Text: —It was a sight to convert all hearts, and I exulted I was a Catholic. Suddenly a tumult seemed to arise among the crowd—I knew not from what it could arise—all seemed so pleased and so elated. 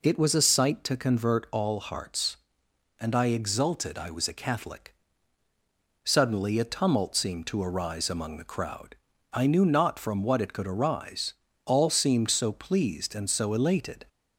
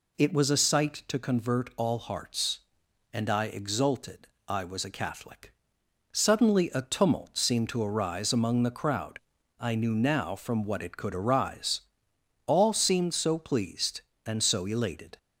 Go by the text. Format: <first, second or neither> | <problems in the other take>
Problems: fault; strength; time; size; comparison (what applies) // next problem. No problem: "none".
first | pauses between "exulted" and "I"; slight; at 4.2 s; 0.18 s long // says "now" for "not"; at 9.9 s